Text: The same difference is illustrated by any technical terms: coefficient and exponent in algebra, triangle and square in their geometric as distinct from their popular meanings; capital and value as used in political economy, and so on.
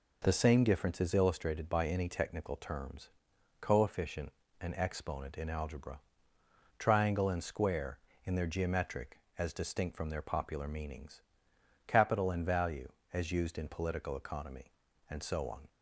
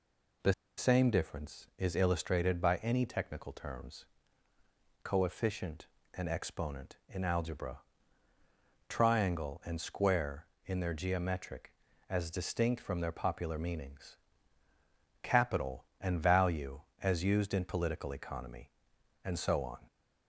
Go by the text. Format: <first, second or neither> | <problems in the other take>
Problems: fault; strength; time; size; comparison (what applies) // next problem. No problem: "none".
first | pauses between "The" and "same"; slight; at 0.5 s; 0.25 s long